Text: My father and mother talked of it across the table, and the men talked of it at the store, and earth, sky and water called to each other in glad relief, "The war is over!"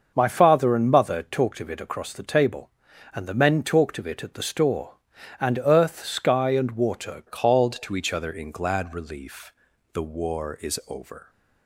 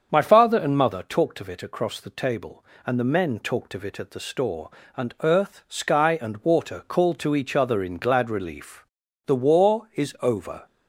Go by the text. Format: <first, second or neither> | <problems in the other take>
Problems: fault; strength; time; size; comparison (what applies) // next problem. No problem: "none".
second | starts louder than the rest; until 1.1 s; 6.5 dB; also in the second // changes voice at "called"; from 7.2 s on; 4.0 s long